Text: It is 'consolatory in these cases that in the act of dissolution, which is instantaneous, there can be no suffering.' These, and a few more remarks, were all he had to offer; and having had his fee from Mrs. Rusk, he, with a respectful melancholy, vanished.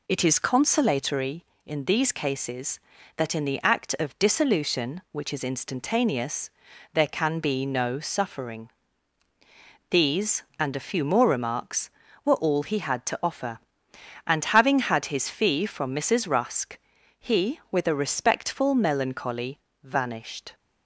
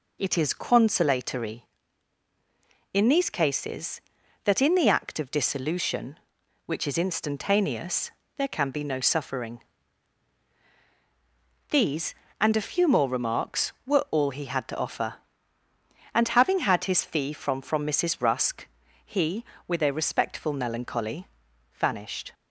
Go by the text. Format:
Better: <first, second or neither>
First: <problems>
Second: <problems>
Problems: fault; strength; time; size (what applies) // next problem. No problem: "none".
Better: first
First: none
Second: says "from" twice; at 17.6 s